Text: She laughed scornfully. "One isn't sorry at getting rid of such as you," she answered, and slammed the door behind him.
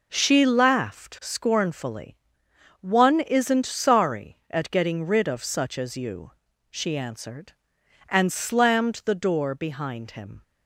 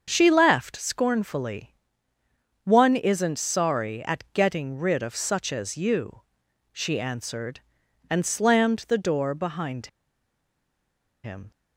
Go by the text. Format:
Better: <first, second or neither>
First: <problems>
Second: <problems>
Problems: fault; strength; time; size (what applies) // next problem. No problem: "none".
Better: first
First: none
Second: starts louder than the rest; until 1.0 s; 7 dB // pauses between "behind" and "him"; strong; at 9.8 s; 1.3 s long